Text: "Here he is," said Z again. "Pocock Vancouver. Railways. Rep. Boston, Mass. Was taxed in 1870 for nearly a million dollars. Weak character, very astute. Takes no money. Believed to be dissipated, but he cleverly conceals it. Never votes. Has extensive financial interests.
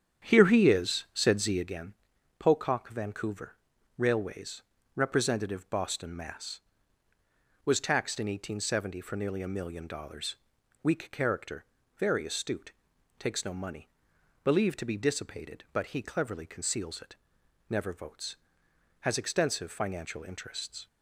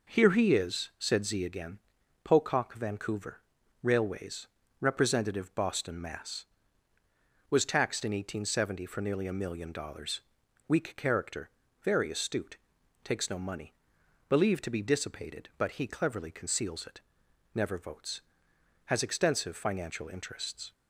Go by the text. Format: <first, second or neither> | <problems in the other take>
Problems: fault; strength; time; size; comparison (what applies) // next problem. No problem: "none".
second | starts louder than the rest; strong; until 1.9 s; 9 dB